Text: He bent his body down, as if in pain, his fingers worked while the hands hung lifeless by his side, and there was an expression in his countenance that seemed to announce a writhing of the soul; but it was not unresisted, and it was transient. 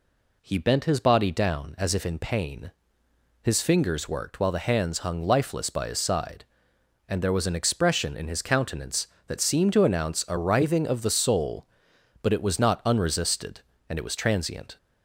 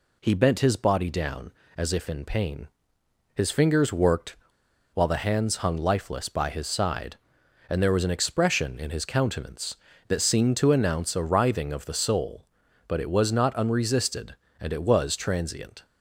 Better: first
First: none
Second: pauses between "worked" and "while"; noticeable; at 4.3 s; 0.57 s long

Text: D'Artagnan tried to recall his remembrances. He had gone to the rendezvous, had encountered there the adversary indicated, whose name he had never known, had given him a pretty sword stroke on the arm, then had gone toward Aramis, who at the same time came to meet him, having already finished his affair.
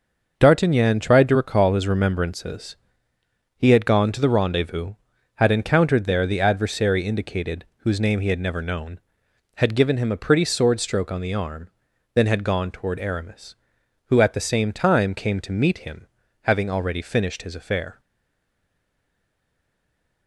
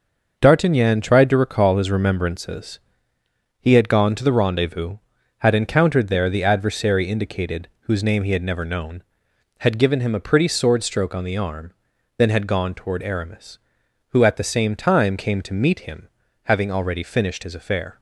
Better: second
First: starts louder than the rest; until 1.3 s; 6 dB // stays silent after the last word; from 17.9 s on; 2.3 s long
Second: starts louder than the rest; until 1.3 s; 6 dB

